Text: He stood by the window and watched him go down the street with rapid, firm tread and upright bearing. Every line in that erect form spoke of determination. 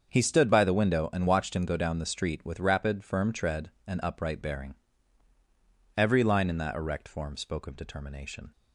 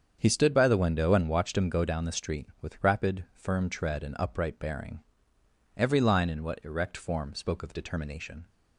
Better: first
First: starts louder than the rest; until 1.1 s; 7 dB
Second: starts louder than the rest; strong; until 1.2 s; 7.5 dB // says "what" for "that"; at 6.4 s

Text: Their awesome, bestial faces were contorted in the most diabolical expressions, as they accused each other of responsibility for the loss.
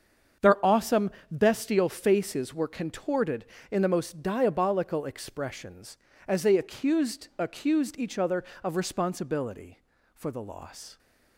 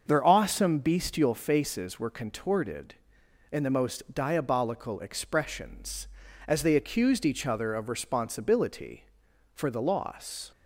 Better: second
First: starts louder than the rest; strong; until 1.5 s; 7 dB // says "accused" twice; at 7.3 s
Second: starts louder than the rest; until 1.0 s; 6.5 dB

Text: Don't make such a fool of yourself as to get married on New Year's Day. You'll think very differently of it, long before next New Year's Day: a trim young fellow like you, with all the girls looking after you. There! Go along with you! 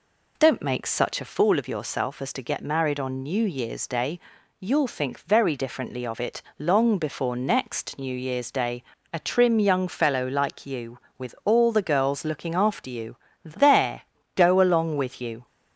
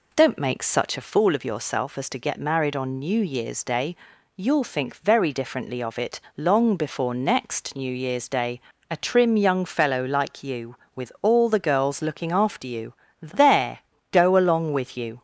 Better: neither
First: none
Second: none

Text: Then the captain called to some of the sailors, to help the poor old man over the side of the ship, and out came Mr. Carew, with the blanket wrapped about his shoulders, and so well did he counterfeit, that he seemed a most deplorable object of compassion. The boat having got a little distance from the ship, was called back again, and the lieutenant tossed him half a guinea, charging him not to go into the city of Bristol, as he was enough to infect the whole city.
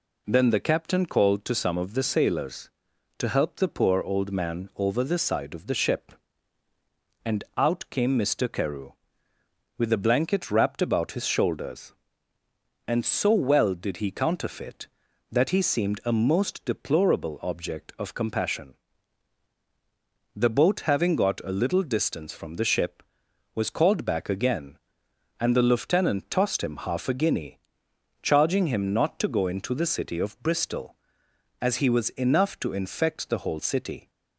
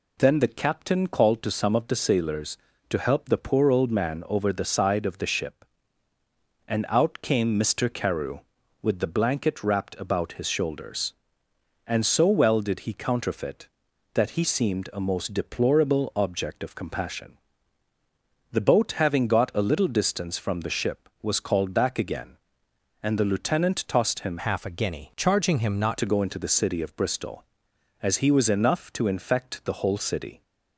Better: first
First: none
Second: changes voice from "half" to "not"; from 24.3 to 25.9 s; 1.6 s long

